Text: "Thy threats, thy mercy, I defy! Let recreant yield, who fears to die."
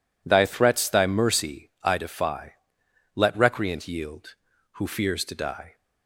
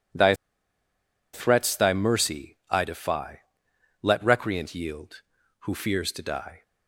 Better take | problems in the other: first | pauses between "Thy" and "threats"; at 0.3 s; 1.0 s long

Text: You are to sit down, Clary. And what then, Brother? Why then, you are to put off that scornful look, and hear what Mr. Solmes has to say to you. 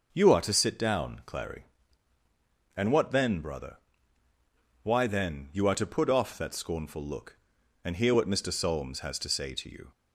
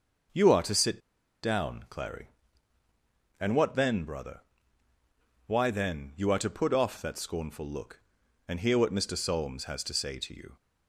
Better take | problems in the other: first | starts louder than the rest; noticeable; until 1.7 s; 6 dB // pauses between "sit" and "down"; at 0.9 s; 0.43 s long

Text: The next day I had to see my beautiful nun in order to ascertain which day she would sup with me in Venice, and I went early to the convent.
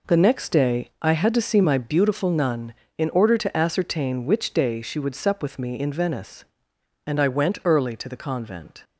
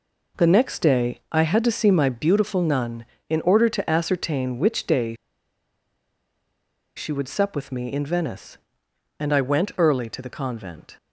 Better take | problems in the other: first | pauses between "day" and "she"; strong; at 5.1 s; 1.8 s long

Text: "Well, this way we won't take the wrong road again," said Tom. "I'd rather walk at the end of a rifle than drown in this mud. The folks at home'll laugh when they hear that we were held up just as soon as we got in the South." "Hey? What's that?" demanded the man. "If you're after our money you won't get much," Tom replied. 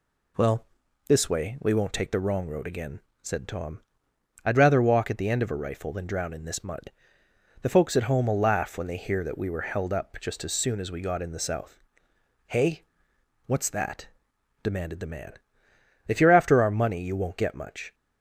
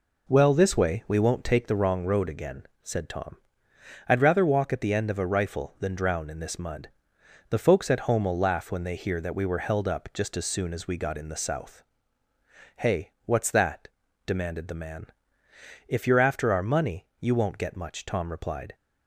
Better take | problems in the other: second | stops before "Tom replied"; at 17.9 s

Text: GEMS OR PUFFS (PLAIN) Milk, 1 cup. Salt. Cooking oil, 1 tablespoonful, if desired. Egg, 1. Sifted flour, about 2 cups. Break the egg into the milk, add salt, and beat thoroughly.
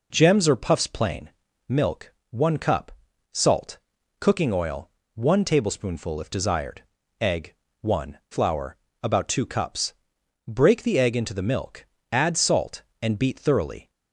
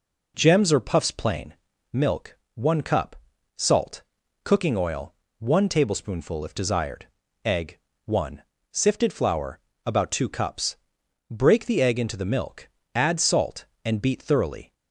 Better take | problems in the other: second | skips "Sifted"; at 8.2 s

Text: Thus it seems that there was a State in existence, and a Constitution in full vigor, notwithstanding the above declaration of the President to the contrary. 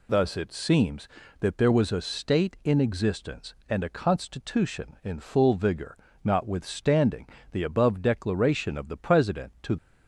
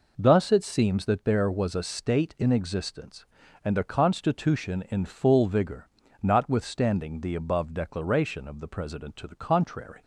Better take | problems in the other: second | pauses between "notwithstanding" and "the"; slight; at 7.2 s; 0.24 s long // stops before "the contrary"; at 9.7 s

